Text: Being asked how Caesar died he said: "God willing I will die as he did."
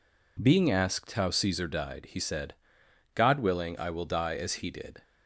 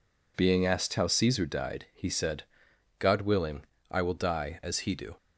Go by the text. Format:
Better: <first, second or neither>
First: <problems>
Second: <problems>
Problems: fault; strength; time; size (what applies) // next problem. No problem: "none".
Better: first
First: none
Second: pauses between "willing" and "I"; slight; at 3.6 s; 0.26 s long // says "do" for "did"; at 4.9 s